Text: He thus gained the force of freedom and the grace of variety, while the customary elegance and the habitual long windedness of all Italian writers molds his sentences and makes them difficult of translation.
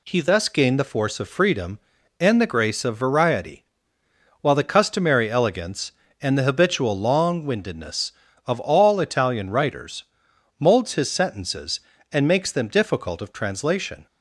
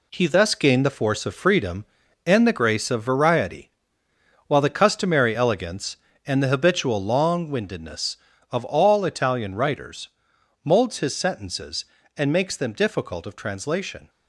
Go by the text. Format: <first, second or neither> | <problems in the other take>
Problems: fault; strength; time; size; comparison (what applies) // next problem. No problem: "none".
first | gets quieter; strong; throughout; 7.5 dB // pauses between "writers" and "molds"; noticeable; at 10.0 s; 0.56 s long; noticeable in the first